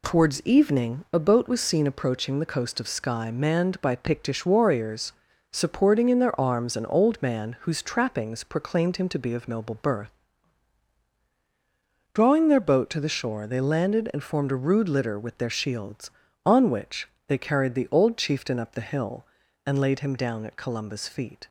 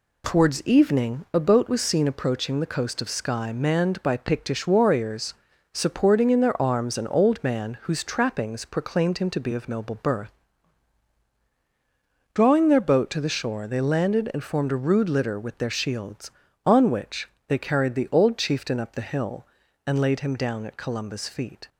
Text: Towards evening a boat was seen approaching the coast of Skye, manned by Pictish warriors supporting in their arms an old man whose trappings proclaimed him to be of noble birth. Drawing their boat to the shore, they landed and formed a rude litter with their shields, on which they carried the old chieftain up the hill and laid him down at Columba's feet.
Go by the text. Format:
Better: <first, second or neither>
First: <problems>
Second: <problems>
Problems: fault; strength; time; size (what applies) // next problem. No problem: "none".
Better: neither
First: pauses between "warriors" and "supporting"; slight; at 5.1 s; 0.36 s long // pauses between "which" and "they"; slight; at 17.0 s; 0.20 s long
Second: pauses between "warriors" and "supporting"; slight; at 5.3 s; 0.36 s long // pauses between "which" and "they"; slight; at 17.2 s; 0.20 s long